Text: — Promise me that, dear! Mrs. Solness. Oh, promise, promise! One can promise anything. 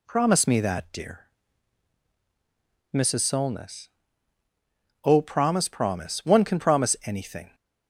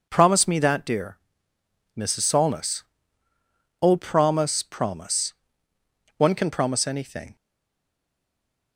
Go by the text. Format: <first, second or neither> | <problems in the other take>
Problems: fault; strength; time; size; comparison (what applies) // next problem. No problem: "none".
first | stays silent after the last word; noticeable; from 7.3 s on; 1.4 s long